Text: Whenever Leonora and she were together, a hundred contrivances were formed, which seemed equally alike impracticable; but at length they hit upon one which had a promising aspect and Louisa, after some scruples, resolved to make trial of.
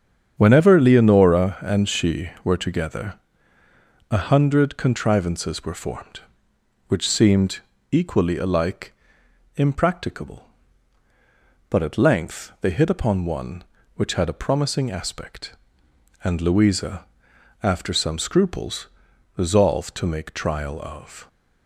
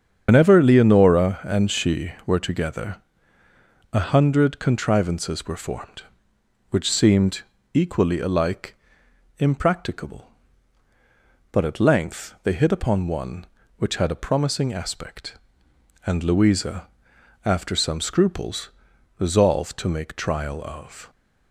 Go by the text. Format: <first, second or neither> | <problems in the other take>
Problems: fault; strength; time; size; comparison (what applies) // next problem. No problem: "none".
first | loses the start of "Whenever"; at 0.2 s; 90 ms // starts louder than the rest; strong; until 1.2 s; 7.5 dB; strong in the first // pauses between "seemed" and "equally"; slight; at 7.3 s; 0.32 s long; slight in the first // pauses between "alike" and "impracticable"; noticeable; at 8.7 s; 0.62 s long; noticeable in the first